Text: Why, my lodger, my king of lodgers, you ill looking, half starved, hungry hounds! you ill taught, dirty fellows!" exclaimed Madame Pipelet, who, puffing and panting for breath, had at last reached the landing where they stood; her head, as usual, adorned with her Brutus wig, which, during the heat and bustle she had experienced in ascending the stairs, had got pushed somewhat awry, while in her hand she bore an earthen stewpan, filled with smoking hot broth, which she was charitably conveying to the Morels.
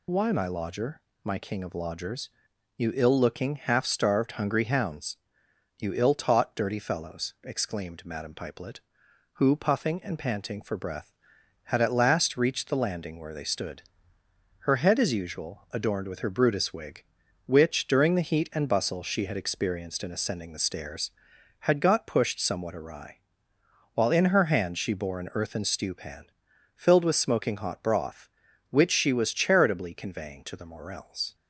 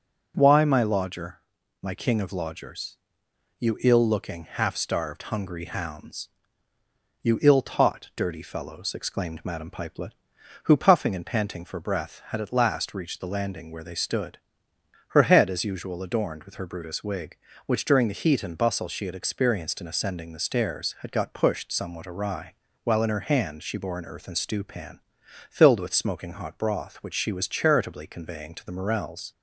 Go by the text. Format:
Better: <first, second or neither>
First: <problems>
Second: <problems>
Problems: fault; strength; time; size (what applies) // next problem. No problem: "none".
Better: second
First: loses the start of "Why"; at 0.0 s; 35 ms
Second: none